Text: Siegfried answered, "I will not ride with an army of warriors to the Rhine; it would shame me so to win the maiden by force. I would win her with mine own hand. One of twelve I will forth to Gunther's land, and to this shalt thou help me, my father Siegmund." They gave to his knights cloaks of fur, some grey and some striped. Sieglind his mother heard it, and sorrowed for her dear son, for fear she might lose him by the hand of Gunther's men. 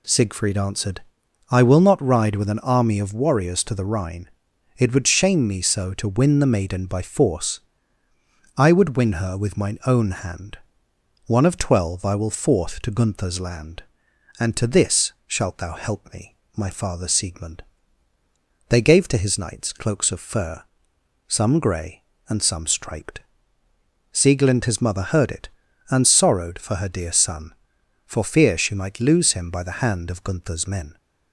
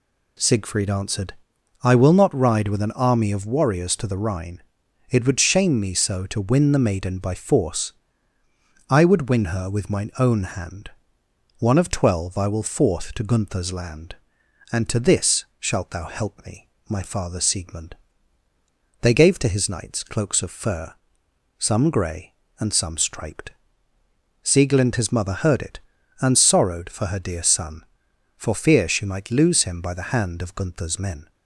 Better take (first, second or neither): neither